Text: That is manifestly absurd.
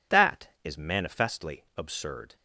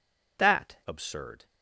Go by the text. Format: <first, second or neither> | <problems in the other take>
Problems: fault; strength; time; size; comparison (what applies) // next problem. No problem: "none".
first | skips "is manifestly"; at 0.8 s